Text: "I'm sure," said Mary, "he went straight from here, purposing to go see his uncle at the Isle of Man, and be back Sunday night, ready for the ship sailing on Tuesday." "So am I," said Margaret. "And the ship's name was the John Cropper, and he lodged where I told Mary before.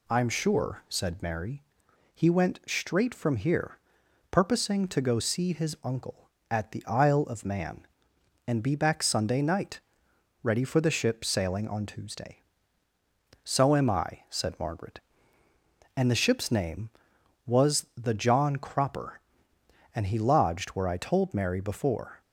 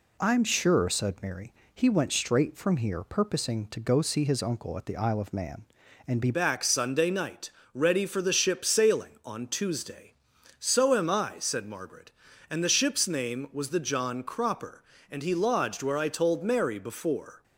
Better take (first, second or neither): first